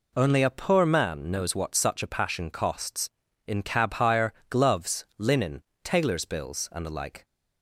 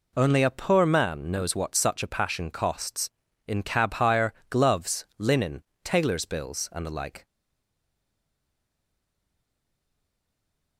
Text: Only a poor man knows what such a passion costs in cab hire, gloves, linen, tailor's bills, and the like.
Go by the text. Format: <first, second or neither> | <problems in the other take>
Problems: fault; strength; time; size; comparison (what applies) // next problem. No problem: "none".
first | stays silent after the last word; strong; from 7.2 s on; 3.5 s long